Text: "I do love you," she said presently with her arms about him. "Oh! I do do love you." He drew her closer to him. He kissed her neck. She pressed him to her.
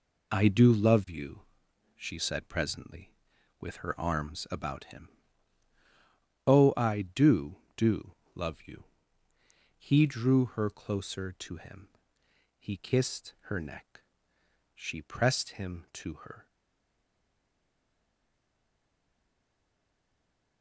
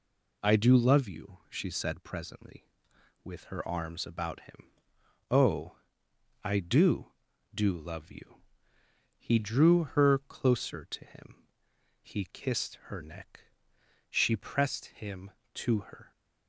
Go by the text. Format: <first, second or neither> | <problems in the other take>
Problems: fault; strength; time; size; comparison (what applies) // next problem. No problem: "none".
second | pauses between "do" and "love"; slight; at 8.1 s; 0.20 s long // stays silent after the last word; strong; from 16.4 s on; 4.2 s long